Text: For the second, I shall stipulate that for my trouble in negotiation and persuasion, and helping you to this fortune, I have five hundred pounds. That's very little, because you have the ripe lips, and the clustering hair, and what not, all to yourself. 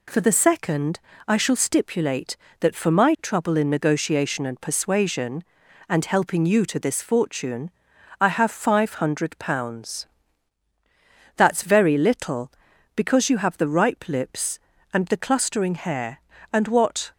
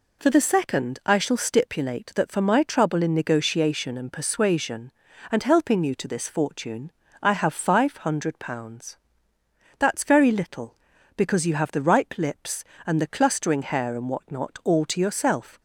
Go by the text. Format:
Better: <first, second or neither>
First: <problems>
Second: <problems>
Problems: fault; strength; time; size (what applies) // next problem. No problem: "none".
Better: second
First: stops before "not all to yourself"; at 17.1 s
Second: none